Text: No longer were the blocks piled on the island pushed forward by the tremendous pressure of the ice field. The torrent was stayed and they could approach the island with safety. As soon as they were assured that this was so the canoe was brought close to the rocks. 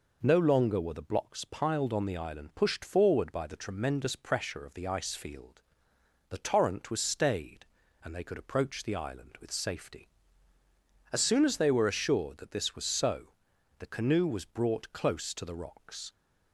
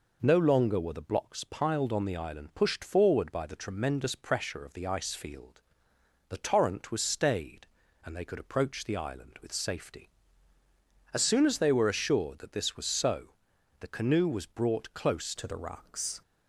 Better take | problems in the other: first | pauses between "so" and "the"; noticeable; at 13.3 s; 0.46 s long; noticeable in the first // changes voice at "to"; from 15.3 s on; 0.9 s long

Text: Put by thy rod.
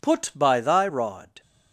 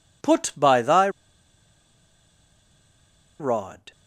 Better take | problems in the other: first | pauses between "thy" and "rod"; strong; at 1.0 s; 2.3 s long

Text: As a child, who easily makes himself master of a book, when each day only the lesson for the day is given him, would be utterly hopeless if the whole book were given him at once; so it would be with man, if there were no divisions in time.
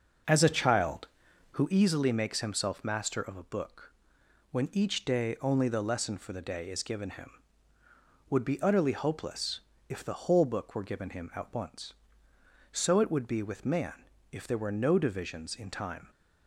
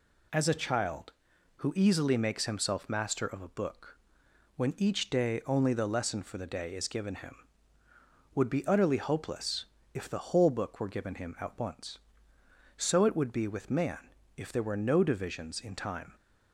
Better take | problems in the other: second | starts louder than the rest; noticeable; until 1.8 s; 6 dB // pauses between "hopeless" and "if"; slight; at 9.6 s; 0.28 s long; slight in the second

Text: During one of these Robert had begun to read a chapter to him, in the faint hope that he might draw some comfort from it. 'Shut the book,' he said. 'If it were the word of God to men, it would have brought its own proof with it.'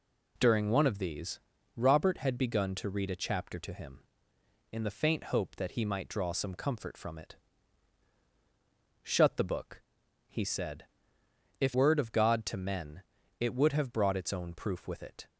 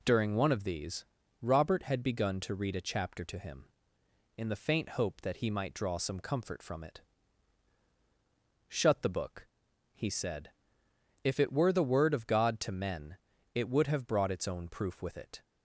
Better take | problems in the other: second | pauses between "these" and "Robert"; at 1.3 s; 0.38 s long; also in the second // skips "it were the"; at 11.7 s

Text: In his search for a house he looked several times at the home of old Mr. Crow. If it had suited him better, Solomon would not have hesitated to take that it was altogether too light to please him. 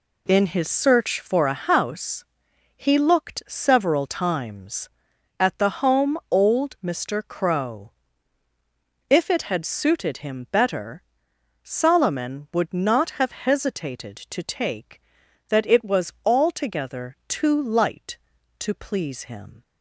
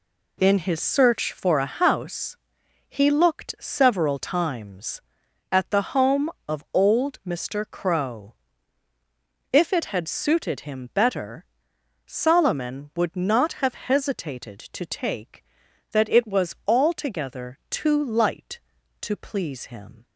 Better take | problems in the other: second | pauses between "house" and "he"; noticeable; at 2.2 s; 0.50 s long; noticeable in the second // skips "of"; at 6.2 s

